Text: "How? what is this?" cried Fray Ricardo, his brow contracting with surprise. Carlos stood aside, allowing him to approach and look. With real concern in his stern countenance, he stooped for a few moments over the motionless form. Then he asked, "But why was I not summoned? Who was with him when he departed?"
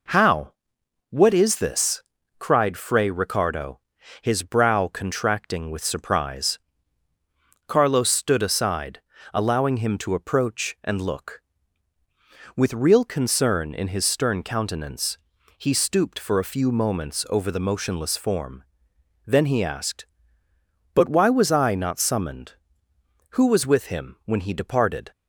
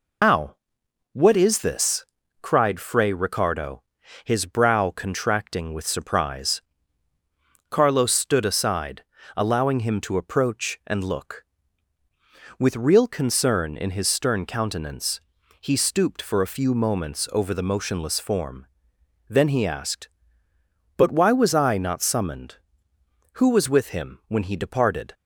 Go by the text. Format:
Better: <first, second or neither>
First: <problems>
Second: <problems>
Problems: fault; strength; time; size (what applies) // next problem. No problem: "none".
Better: first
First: none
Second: loses the start of "How"; at 0.2 s; 120 ms